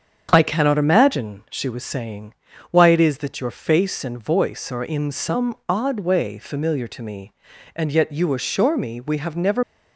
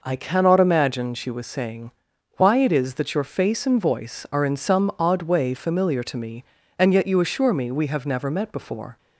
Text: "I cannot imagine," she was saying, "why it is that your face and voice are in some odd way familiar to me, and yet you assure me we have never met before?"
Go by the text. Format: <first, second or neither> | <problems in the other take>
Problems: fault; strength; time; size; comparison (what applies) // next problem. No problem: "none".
second | starts louder than the rest; strong; until 1.3 s; 7.5 dB // stops before "met before"; at 9.6 s